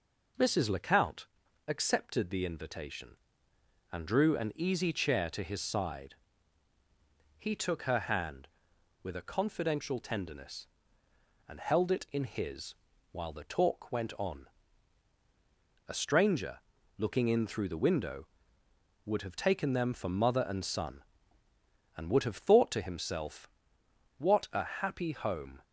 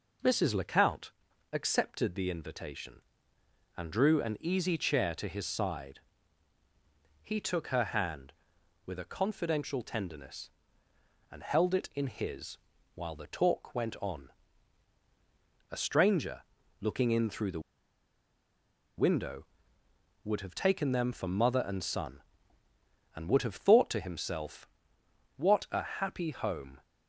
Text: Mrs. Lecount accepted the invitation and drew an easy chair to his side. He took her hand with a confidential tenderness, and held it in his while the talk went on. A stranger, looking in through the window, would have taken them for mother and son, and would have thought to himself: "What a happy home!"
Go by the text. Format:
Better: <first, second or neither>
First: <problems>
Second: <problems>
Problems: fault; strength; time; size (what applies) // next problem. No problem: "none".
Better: first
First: pauses between "Lecount" and "accepted"; at 1.2 s; 0.42 s long // pauses between "his" and "while"; at 12.7 s; 0.38 s long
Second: pauses between "Lecount" and "accepted"; at 1.1 s; 0.42 s long // pauses between "his" and "while"; at 12.5 s; 0.38 s long // pauses between "the" and "window"; strong; at 17.5 s; 1.3 s long